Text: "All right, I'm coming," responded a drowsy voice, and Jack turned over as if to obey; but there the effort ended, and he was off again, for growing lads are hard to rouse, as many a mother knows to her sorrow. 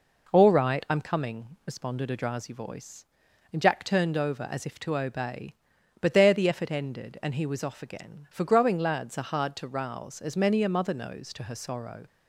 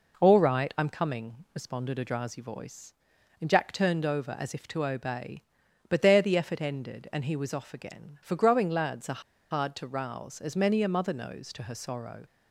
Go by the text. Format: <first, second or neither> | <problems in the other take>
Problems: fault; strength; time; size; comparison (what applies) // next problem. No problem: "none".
first | pauses between "are" and "hard"; slight; at 9.1 s; 0.31 s long